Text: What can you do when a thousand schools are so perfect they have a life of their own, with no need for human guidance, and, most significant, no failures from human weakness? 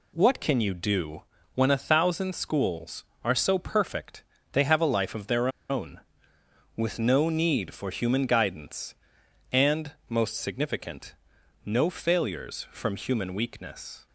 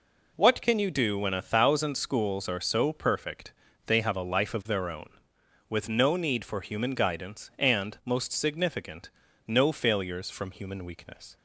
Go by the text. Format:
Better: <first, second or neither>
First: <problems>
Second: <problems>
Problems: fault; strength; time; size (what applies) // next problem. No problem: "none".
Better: second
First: pauses between "do" and "when"; slight; at 1.2 s; 0.34 s long // pauses between "perfect" and "they"; slight; at 4.2 s; 0.30 s long // pauses between "their" and "own"; slight; at 5.4 s; 0.21 s long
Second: pauses between "perfect" and "they"; slight; at 3.5 s; 0.34 s long